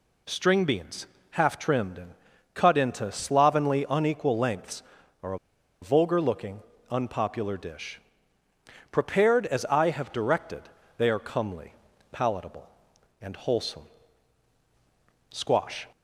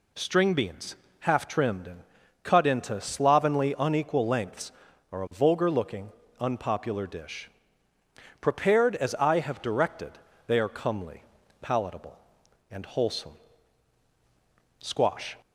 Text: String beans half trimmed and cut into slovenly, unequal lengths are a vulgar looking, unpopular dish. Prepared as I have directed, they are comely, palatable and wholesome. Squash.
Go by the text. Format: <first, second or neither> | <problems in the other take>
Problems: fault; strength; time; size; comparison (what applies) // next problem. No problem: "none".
second | pauses between "beans" and "half"; slight; at 1.0 s; 0.24 s long; slight in the second // pauses between "and" and "cut"; at 2.1 s; 0.42 s long; also in the second // pauses between "a" and "vulgar"; at 5.3 s; 0.43 s long